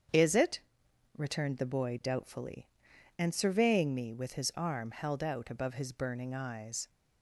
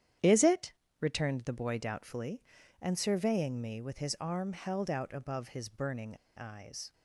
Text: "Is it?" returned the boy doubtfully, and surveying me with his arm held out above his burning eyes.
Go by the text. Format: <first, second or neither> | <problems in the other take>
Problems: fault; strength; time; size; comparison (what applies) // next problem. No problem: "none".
first | starts louder than the rest; strong; until 1.4 s; 10 dB; strong in the first // pauses between "burning" and "eyes"; slight; at 6.1 s; 0.19 s long